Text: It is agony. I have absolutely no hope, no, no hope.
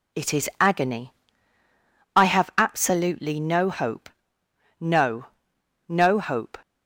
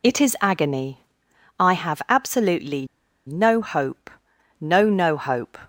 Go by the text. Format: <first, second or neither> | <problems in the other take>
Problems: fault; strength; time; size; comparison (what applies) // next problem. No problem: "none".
first | pauses between "absolutely" and "no"; at 2.8 s; 0.40 s long